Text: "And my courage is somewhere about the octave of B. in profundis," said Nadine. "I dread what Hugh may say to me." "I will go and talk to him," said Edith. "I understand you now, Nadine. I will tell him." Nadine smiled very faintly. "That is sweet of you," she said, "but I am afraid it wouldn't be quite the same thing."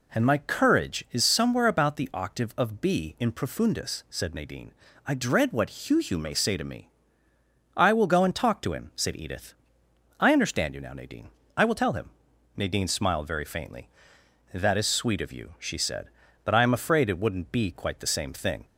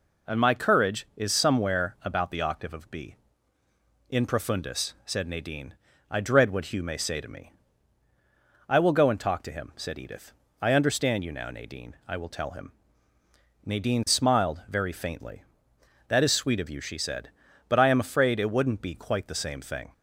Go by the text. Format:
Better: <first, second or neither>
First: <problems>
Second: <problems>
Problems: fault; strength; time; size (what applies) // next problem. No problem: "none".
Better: second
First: says "Hugh" twice; at 5.9 s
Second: none